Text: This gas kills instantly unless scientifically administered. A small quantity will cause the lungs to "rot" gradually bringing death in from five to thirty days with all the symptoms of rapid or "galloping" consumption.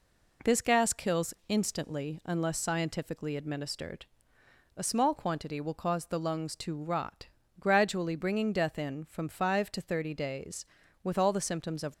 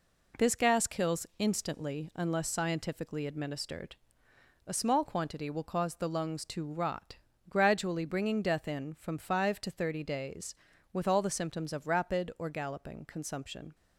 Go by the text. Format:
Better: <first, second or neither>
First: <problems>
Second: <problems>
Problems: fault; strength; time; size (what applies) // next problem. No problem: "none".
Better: second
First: pauses between "rot" and "gradually"; slight; at 7.2 s; 0.34 s long // stops before "rapid or galloping consumption"; at 11.9 s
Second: pauses between "rot" and "gradually"; slight; at 7.1 s; 0.34 s long